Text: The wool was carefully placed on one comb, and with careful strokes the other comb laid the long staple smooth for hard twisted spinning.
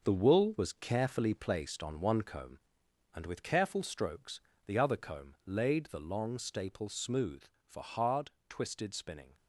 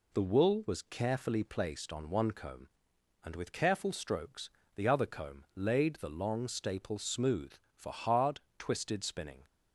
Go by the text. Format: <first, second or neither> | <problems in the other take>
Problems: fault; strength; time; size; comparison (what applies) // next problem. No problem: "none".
second | gets quieter; strong; throughout; 7.5 dB // pauses between "strokes" and "the"; slight; at 4.4 s; 0.26 s long; slight in the second // pauses between "hard" and "twisted"; slight; at 8.3 s; 0.18 s long; slight in the second